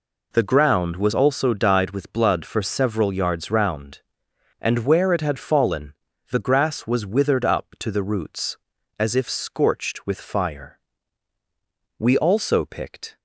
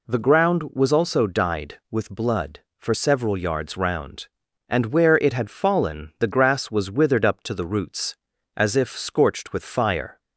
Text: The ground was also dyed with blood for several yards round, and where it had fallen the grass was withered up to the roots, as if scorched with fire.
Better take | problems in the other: second | pauses between "fallen" and "the"; at 5.9 s; 0.38 s long // goes on to say "We also picked"; noticeable; from 11.9 s on; 1.2 s long

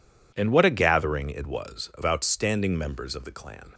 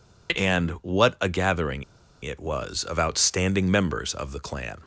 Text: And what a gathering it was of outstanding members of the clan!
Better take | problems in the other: first | pauses between "gathering" and "it"; at 1.8 s; 0.39 s long

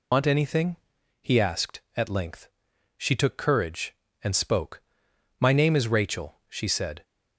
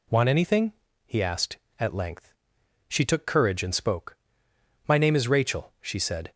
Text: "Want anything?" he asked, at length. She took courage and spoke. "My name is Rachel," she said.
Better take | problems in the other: second | loses the start of "Want"; at 0.1 s; 90 ms

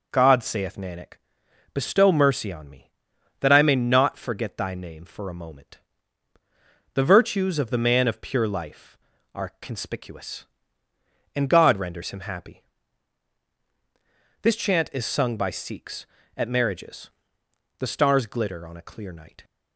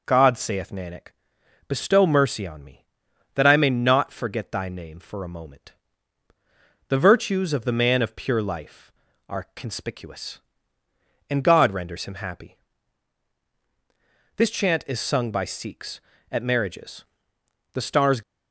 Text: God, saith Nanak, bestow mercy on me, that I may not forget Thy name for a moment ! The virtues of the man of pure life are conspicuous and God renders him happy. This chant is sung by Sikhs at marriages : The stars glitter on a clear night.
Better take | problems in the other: first | stops before "glitter on a clear night"; at 18.2 s

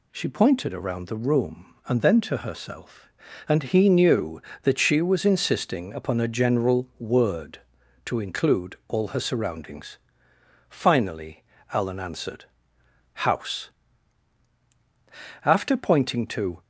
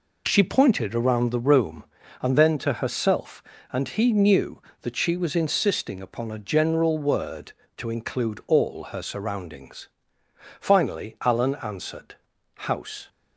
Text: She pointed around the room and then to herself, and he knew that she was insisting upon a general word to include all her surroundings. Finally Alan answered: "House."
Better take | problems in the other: second | pauses between "Finally" and "Alan"; slight; at 11.4 s; 0.30 s long // goes on to say "After pointing to"; noticeable; from 15.4 s on; 1.1 s long

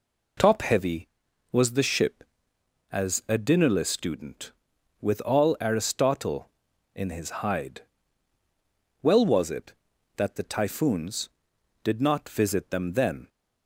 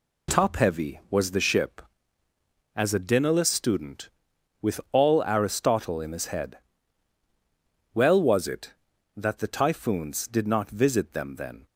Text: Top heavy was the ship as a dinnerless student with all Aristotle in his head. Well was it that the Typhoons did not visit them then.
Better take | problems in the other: second | says "hide" for "head"; at 7.4 s

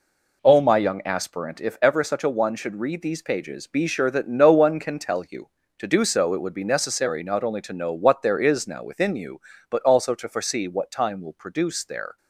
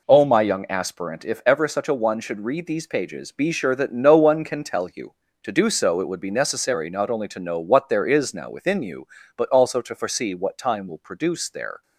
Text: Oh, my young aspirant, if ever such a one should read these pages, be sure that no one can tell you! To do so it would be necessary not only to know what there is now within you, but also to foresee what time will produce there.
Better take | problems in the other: neither | none

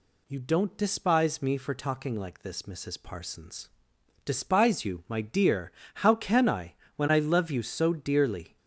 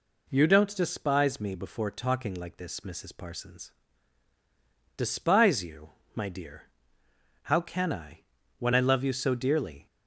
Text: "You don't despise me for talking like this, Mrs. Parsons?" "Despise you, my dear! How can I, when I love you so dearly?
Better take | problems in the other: first | says "before" for "for"; at 1.5 s

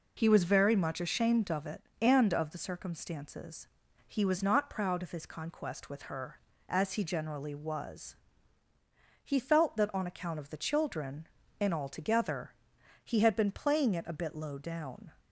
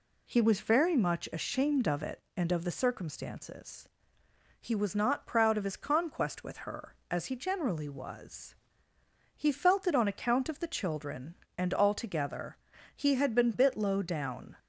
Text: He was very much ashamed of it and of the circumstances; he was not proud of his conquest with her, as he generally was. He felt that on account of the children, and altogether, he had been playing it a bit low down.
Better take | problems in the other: first | skips "playing it a"; at 13.5 s

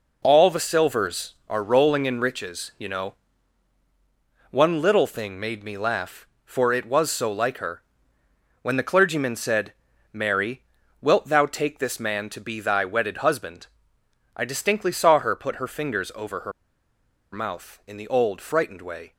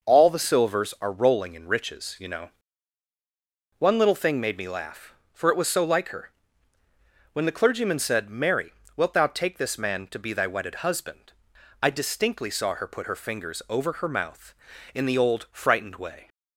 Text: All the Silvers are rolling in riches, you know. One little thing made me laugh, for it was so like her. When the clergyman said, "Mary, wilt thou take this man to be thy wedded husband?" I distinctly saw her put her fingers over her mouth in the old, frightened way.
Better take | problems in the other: second | pauses between "her" and "mouth"; noticeable; at 16.5 s; 0.81 s long

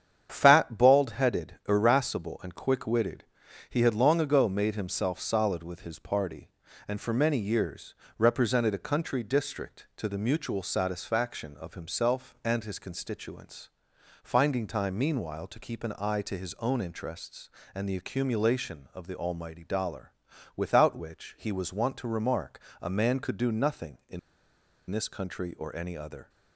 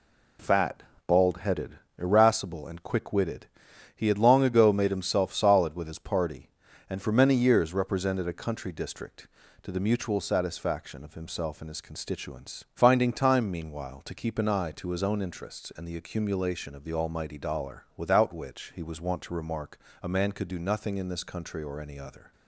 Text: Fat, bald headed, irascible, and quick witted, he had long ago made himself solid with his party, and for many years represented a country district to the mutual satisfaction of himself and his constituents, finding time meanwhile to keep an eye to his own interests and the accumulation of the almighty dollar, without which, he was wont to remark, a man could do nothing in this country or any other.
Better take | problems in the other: second | starts louder than the rest; strong; until 1.3 s; 8.5 dB // pauses between "years" and "represented"; slight; at 7.9 s; 0.22 s long // pauses between "in" and "this"; noticeable; at 24.1 s; 0.71 s long

